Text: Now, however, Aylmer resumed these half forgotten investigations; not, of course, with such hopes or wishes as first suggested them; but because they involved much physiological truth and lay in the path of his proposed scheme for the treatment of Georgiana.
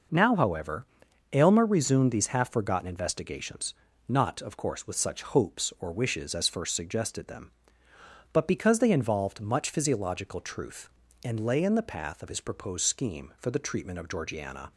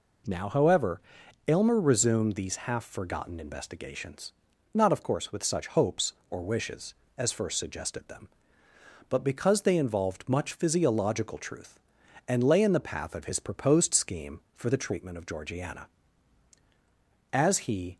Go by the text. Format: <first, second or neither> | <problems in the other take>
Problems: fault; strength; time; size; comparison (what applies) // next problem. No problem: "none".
first | goes on to say "As he"; noticeable; from 17.3 s on; 0.64 s long